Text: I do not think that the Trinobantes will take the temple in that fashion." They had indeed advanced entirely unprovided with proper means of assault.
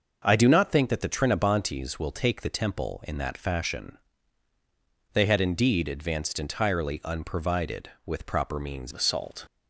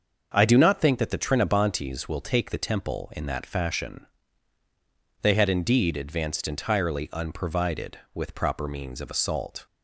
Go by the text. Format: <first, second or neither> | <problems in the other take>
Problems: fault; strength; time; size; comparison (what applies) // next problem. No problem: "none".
second | starts louder than the rest; until 1.2 s; 6.5 dB; also in the second // changes voice at "of"; from 8.9 s on; 0.5 s long